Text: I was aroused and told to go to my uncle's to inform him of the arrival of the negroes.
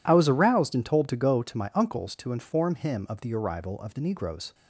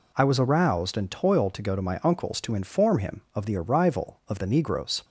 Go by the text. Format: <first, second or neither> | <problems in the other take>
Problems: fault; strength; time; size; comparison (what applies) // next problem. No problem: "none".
first | says "toiled" for "told"; at 1.1 s